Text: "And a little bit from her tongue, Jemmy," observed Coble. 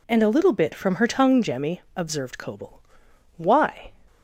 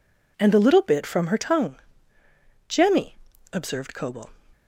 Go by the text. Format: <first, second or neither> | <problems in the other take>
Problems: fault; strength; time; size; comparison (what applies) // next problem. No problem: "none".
second | goes on to say "Why"; from 3.3 s on; 0.54 s long